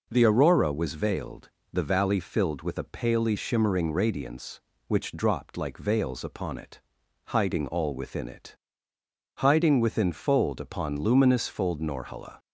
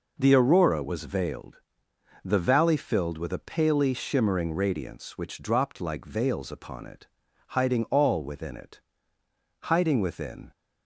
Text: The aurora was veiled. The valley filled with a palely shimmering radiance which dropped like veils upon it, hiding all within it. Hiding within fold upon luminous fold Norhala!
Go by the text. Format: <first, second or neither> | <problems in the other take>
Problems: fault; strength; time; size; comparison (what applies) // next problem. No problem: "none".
first | stops before "fold upon luminous fold Norhala"; at 10.5 s